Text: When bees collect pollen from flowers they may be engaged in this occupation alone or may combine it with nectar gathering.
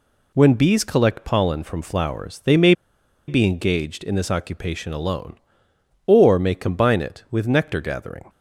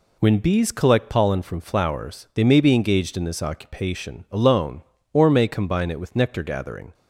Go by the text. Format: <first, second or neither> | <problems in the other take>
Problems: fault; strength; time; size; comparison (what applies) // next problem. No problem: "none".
second | pauses between "may" and "be"; noticeable; at 2.7 s; 0.55 s long